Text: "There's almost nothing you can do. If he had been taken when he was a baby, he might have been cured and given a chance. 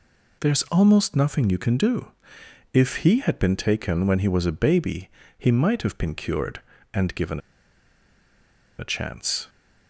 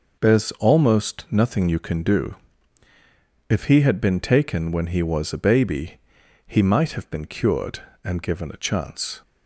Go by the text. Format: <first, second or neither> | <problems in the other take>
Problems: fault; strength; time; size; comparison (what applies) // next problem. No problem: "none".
second | pauses between "given" and "a"; strong; at 7.4 s; 1.3 s long